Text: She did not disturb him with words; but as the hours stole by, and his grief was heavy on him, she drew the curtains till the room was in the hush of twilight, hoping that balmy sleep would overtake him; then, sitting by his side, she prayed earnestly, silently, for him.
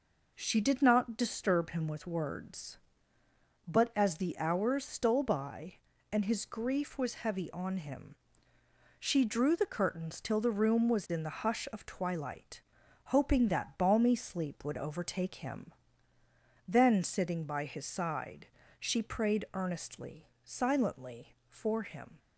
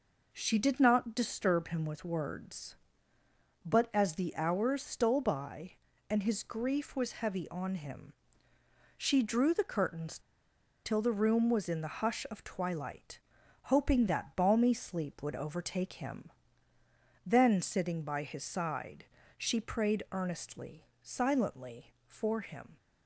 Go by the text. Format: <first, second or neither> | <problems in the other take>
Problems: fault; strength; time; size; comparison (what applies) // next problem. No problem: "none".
first | pauses between "curtains" and "till"; noticeable; at 10.1 s; 0.65 s long